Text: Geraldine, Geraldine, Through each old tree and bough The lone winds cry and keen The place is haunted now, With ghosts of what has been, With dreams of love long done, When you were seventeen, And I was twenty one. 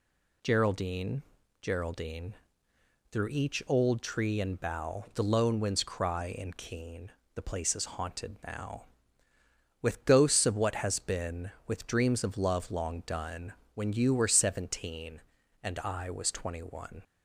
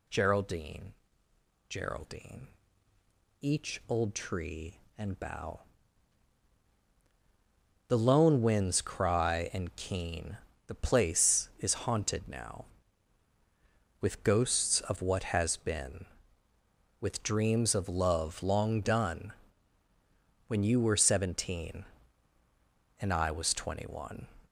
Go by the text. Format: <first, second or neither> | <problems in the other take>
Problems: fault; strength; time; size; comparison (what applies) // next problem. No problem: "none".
first | skips "Through"; at 2.9 s // pauses between "bough" and "The"; strong; at 5.6 s; 2.2 s long // pauses between "keen" and "The"; slight; at 10.3 s; 0.30 s long; slight in the first